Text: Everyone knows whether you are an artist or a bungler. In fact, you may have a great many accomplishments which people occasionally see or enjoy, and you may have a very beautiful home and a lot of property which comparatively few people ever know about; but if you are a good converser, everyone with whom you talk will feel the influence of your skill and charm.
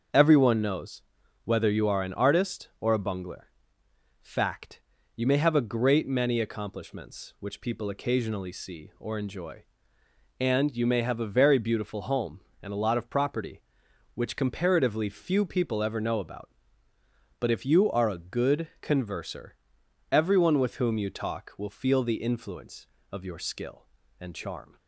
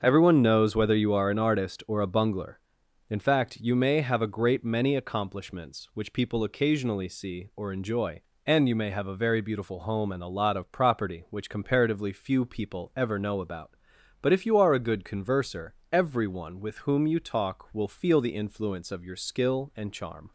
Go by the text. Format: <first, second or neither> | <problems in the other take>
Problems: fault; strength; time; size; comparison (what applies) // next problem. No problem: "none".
second | starts louder than the rest; until 1.5 s; 6.5 dB; also in the second // pauses between "knows" and "whether"; at 1.0 s; 0.42 s long // skips "In"; at 3.8 s